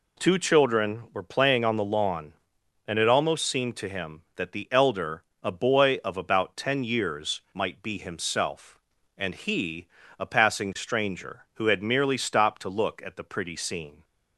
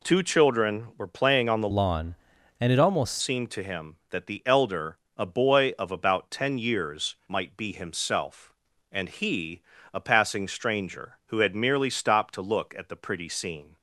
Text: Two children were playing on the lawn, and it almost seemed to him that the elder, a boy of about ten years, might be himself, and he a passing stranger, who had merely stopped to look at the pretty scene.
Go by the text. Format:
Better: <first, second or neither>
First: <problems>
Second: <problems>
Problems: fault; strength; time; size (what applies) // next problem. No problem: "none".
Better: first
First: pauses between "he" and "a"; slight; at 9.8 s; 0.32 s long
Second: changes voice from "lawn" to "almost"; from 1.7 to 3.1 s; 1.4 s long // pauses between "he" and "a"; slight; at 9.6 s; 0.32 s long